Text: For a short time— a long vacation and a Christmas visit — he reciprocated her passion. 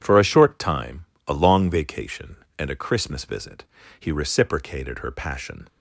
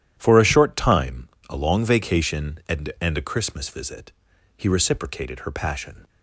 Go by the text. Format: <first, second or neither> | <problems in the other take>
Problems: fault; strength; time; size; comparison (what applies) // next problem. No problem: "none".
first | starts louder than the rest; strong; until 1.1 s; 11 dB // says "and" twice; at 2.9 s